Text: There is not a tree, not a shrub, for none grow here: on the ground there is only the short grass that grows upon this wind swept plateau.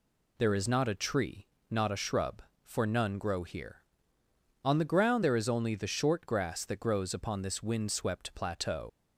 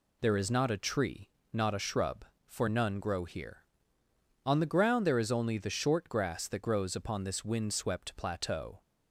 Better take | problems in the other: second | leaves "plateau" unfinished; at 8.8 s; 95 ms

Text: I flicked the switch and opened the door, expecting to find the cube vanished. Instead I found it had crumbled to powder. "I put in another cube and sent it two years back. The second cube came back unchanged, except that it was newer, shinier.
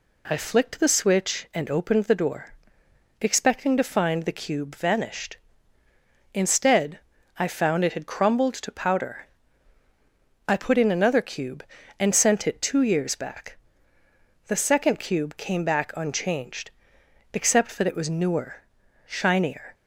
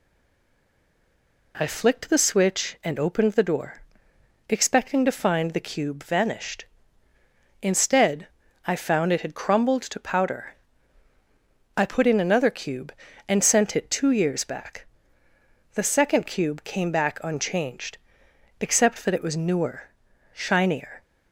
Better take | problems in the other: first | stays silent before the first word; noticeable; until 1.5 s; 1.5 s long // pauses between "Instead" and "I"; at 8.2 s; 0.40 s long; also in the first

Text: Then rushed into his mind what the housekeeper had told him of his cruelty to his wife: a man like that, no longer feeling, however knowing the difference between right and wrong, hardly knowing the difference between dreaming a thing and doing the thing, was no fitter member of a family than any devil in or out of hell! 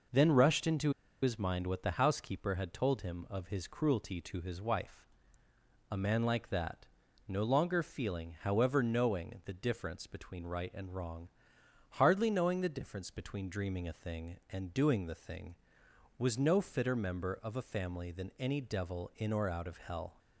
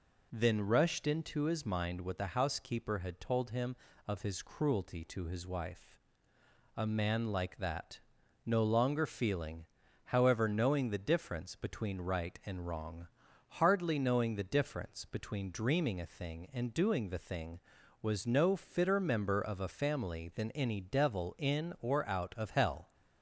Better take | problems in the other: second | pauses between "into" and "his"; slight; at 0.9 s; 0.32 s long

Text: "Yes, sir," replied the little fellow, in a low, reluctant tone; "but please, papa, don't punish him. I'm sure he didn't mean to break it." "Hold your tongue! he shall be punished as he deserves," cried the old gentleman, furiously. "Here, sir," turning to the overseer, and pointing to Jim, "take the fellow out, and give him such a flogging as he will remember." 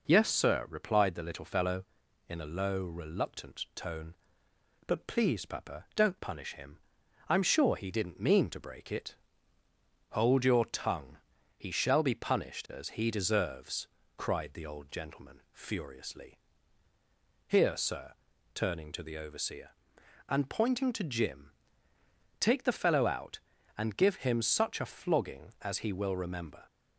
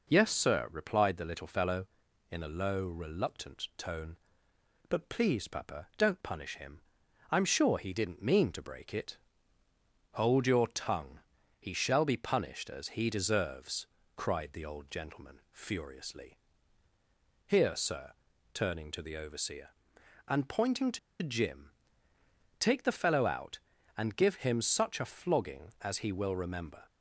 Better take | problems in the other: first | pauses between "to" and "Jim"; slight; at 20.9 s; 0.23 s long

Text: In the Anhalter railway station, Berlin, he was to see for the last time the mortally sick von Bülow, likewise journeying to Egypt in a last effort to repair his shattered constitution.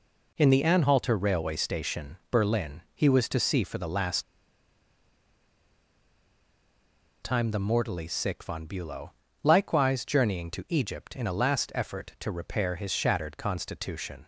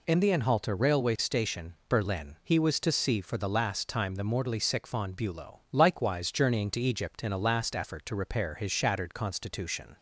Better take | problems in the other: second | pauses between "last" and "time"; strong; at 4.2 s; 3.0 s long

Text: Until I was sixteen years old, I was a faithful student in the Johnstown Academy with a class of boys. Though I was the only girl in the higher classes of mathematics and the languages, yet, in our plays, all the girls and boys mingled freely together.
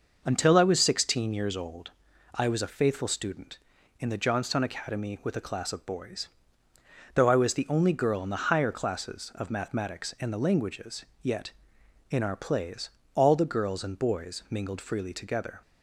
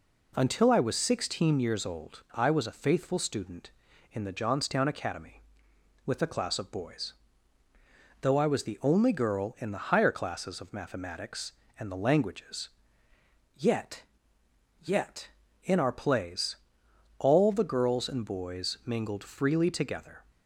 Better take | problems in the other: first | says "yet" twice; at 14.8 s

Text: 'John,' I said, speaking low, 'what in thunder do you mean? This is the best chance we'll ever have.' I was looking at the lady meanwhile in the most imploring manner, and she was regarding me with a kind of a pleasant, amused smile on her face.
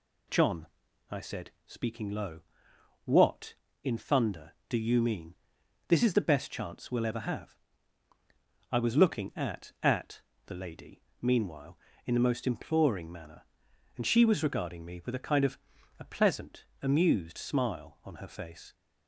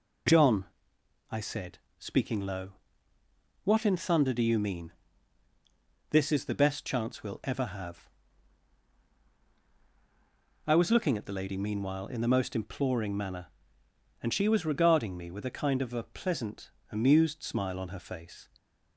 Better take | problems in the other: second | says "at" twice; at 9.8 s // pauses between "lady" and "meanwhile"; slight; at 10.9 s; 0.22 s long // pauses between "of" and "a"; at 15.5 s; 0.40 s long

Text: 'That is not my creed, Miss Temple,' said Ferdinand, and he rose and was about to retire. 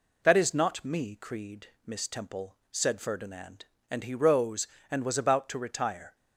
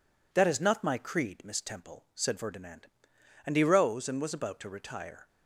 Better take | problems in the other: second | says "me" for "my"; at 0.8 s

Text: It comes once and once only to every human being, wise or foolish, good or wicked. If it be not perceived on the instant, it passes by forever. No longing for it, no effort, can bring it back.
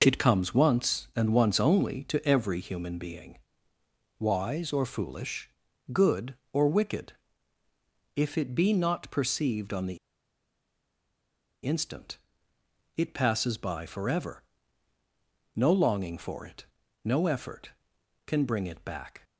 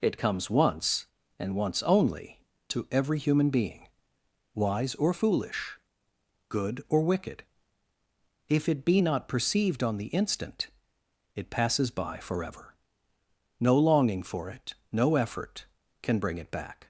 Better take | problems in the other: second | pauses between "the" and "instant"; strong; at 9.9 s; 1.6 s long

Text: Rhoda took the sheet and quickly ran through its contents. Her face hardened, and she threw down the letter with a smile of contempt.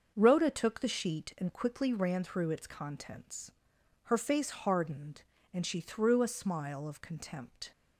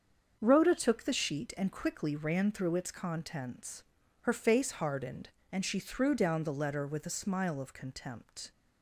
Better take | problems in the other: second | starts louder than the rest; until 1.1 s; 6.5 dB; also in the second // skips "down the letter with"; at 6.2 s

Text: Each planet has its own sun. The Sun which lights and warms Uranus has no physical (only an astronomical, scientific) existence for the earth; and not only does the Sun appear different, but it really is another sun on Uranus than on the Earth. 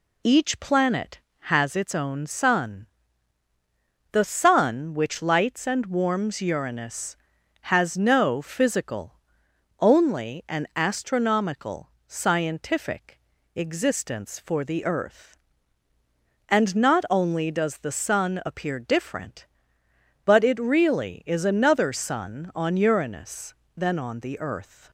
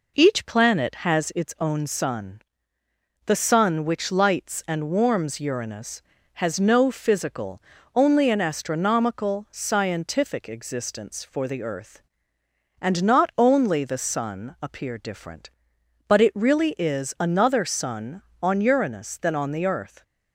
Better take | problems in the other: first | skips "does"; at 13.8 s

